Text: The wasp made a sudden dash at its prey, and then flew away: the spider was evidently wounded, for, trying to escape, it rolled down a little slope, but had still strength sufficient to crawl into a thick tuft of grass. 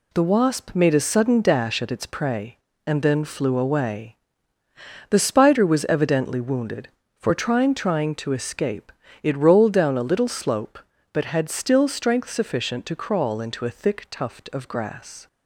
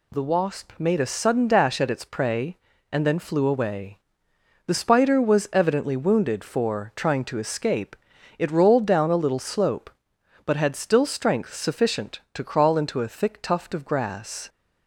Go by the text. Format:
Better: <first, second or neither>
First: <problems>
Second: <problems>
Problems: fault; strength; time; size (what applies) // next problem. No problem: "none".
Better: second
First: says "trying" twice; at 7.7 s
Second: none